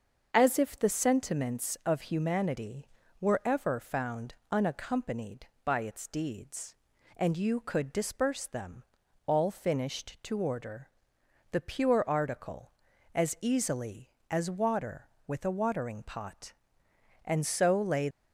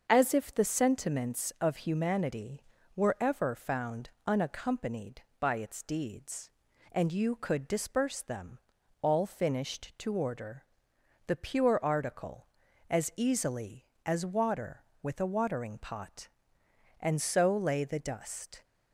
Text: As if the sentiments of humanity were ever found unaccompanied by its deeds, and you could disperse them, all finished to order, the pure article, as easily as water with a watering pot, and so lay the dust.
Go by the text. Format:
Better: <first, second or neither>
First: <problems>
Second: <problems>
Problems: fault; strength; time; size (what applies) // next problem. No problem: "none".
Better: second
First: starts louder than the rest; until 1.3 s; 6.5 dB // pauses between "found" and "unaccompanied"; slight; at 4.3 s; 0.18 s long // stops before "the dust"; at 18.0 s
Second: starts louder than the rest; until 1.1 s; 6.5 dB // pauses between "found" and "unaccompanied"; slight; at 4.0 s; 0.18 s long